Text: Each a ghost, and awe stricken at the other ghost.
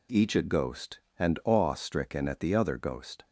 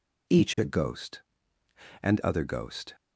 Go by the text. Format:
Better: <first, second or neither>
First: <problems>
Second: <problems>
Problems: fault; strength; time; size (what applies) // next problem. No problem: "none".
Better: first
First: none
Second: skips "awe stricken at the"; at 2.2 s